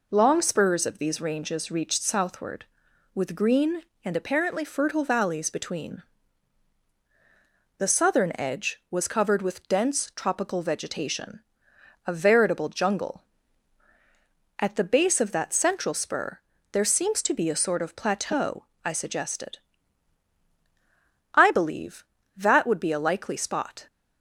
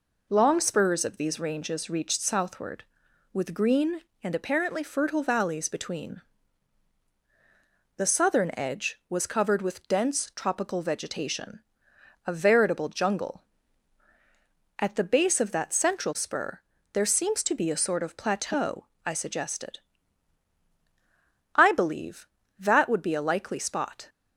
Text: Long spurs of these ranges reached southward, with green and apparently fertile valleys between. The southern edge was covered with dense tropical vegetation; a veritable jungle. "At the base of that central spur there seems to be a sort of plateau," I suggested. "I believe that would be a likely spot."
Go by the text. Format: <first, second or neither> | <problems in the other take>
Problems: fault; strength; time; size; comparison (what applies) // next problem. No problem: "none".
neither | pauses between "spur" and "there"; slight; the same in both